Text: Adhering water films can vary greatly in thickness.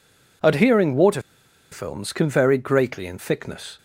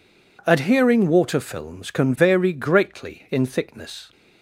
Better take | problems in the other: second | pauses between "water" and "films"; noticeable; at 1.1 s; 0.52 s long

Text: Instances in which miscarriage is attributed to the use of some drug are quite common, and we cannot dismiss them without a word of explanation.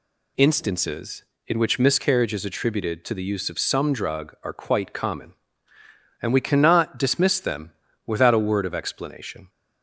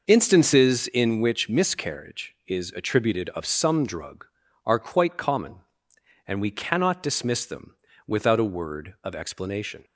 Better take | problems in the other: first | skips "to the use"; at 3.2 s // pauses between "them" and "without"; slight; at 7.7 s; 0.28 s long; slight in the first

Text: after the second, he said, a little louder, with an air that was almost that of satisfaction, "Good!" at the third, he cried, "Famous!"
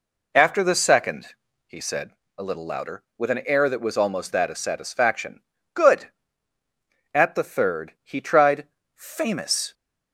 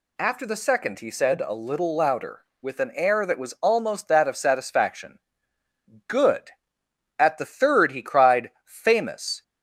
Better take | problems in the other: second | says "tried" for "cried"; at 8.2 s

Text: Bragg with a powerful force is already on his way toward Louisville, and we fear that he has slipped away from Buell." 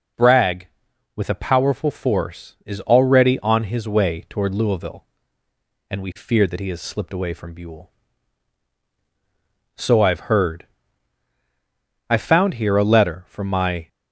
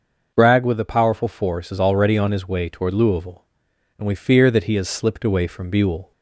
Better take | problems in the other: second | goes on to say "So I've heard I found here a letter from my"; strong; from 9.7 s on; 4.1 s long

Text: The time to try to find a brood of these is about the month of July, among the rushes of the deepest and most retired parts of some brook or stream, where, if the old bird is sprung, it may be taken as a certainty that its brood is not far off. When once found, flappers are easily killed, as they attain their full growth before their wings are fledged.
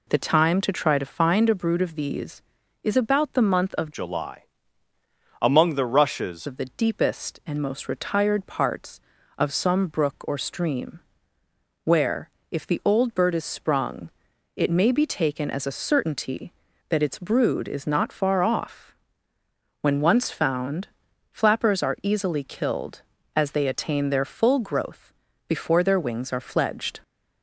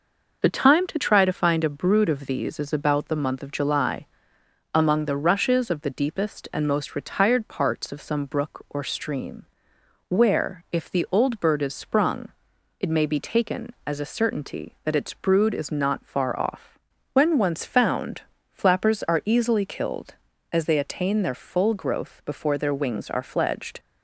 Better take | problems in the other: second | changes voice from "July" to "rushes"; from 3.9 to 6.4 s; 2.5 s long // pauses between "growth" and "before"; slight; at 25.1 s; 0.34 s long

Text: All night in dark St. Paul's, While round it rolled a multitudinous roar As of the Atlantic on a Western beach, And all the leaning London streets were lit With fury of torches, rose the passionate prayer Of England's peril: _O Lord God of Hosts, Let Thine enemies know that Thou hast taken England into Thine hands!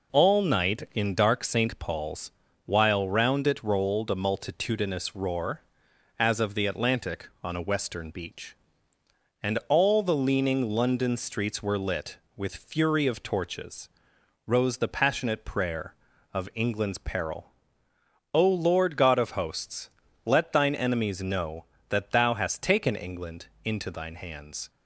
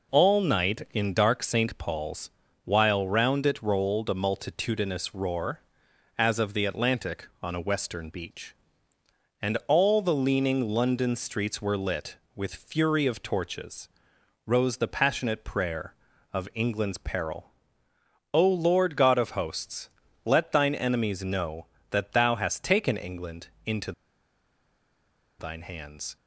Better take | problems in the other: first | pauses between "England" and "into"; slight; at 23.4 s; 0.18 s long; slight in the first // pauses between "into" and "Thine"; strong; at 23.9 s; 1.4 s long

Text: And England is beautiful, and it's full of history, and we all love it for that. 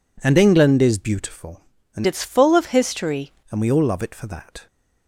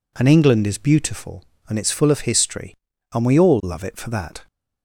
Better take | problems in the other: second | changes voice from "it's" to "history"; from 2.0 to 3.3 s; 1.3 s long

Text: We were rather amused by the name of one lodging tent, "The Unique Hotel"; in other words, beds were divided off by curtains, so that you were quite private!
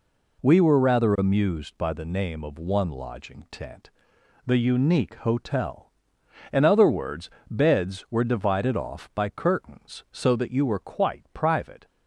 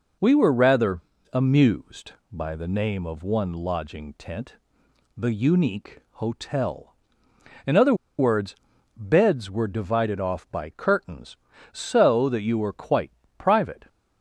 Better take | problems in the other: first | pauses between "rather" and "amused"; slight; at 0.9 s; 0.32 s long // pauses between "other" and "words"; slight; at 7.9 s; 0.24 s long // pauses between "quite" and "private"; slight; at 13.1 s; 0.24 s long

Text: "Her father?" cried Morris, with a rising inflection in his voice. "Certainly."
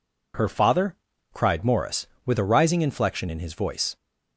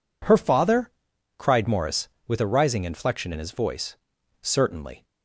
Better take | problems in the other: second | stops before "Certainly"; at 3.9 s

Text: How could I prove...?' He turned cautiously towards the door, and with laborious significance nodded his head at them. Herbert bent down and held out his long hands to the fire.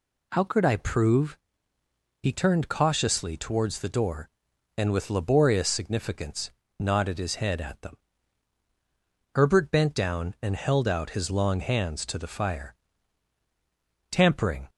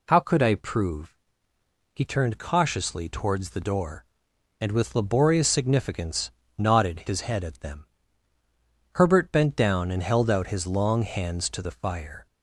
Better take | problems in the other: second | pauses between "significance" and "nodded"; slight; at 6.4 s; 0.28 s long; slight in the second // goes on to say "Tampering"; from 14.1 s on; 0.58 s long

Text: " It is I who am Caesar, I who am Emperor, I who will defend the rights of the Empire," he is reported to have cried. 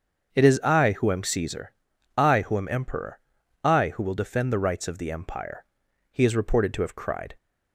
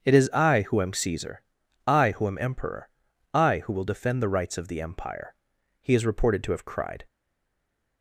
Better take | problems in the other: first | starts louder than the rest; until 1.0 s; 7 dB; also in the first // stays silent after the last word; slight; from 7.0 s on; 1.0 s long

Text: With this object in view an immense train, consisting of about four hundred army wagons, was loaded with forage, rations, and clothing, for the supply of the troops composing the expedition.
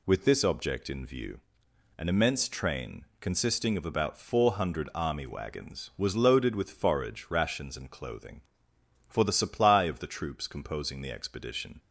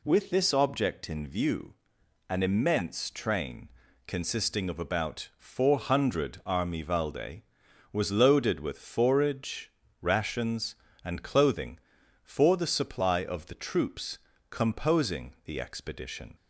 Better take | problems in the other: first | pauses between "view" and "an"; noticeable; at 1.7 s; 0.54 s long; noticeable in the first // says "valde" for "wagons"; at 6.8 s // pauses between "troops" and "composing"; slight; at 14.1 s; 0.32 s long

